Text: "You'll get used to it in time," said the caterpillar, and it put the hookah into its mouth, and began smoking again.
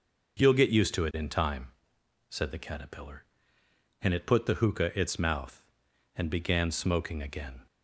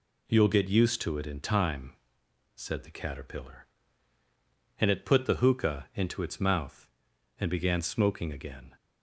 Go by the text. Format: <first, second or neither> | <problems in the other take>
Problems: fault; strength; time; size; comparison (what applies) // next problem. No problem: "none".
second | skips "into"; at 4.9 s